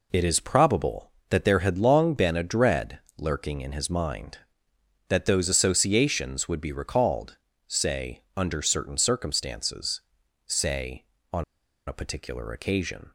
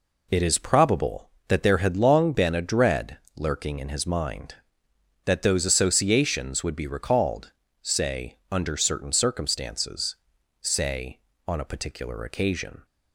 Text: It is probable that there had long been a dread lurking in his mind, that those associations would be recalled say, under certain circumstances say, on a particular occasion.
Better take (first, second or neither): second